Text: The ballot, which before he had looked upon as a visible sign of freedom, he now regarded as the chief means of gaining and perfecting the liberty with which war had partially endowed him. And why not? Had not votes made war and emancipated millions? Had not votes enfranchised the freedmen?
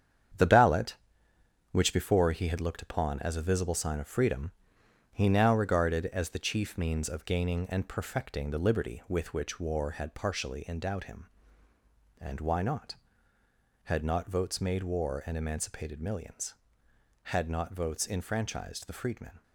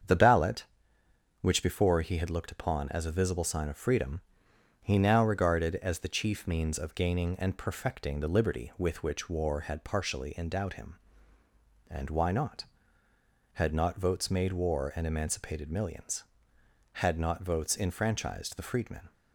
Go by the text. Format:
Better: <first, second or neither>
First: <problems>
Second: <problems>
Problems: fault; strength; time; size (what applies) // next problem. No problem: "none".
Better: second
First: gets quieter; strong; throughout; 8 dB // starts louder than the rest; strong; until 2.1 s; 8.5 dB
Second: starts louder than the rest; strong; until 1.8 s; 7.5 dB